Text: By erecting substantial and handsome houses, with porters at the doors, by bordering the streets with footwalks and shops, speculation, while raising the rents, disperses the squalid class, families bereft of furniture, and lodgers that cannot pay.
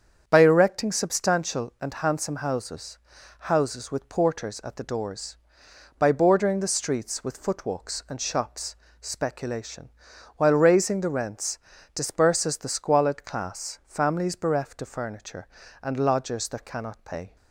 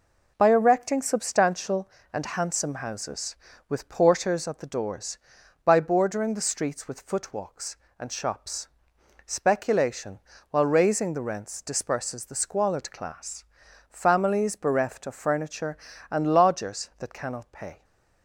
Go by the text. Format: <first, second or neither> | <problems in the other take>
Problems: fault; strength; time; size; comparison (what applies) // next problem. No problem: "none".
second | starts louder than the rest; strong; until 1.2 s; 7.5 dB // says "houses" twice; at 3.4 s